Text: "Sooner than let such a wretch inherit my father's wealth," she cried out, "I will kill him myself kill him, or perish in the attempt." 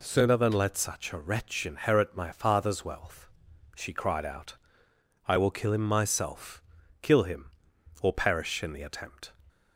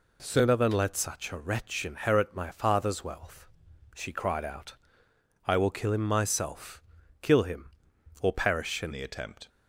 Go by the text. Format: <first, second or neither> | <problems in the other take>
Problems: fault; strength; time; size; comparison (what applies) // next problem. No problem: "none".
first | pauses between "myself" and "kill"; at 6.8 s; 0.40 s long; also in the first // changes voice at "the"; from 8.9 s on; 0.5 s long